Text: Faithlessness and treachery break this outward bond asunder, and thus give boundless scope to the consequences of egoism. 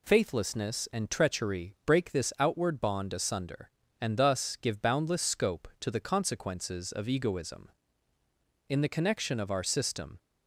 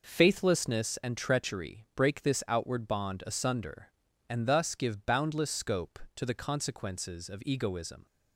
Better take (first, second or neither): second